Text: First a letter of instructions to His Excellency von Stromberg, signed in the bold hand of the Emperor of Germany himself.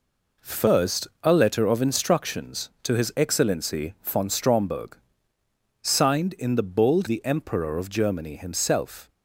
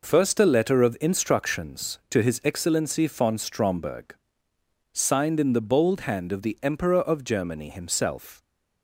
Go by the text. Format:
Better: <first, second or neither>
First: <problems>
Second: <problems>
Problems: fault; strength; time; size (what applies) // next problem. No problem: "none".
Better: second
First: pauses between "First" and "a"; slight; at 1.0 s; 0.16 s long // skips "hand of"; at 7.0 s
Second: none